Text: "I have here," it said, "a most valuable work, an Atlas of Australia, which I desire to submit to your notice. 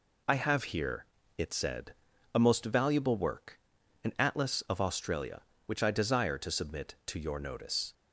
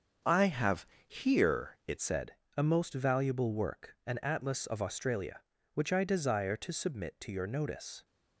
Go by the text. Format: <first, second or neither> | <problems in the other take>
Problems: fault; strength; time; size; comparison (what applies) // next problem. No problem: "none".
first | starts louder than the rest; until 1.4 s; 6.5 dB // pauses between "have" and "here"; slight; at 0.8 s; 0.18 s long // changes voice at "said"; from 1.9 s on; 6.1 s long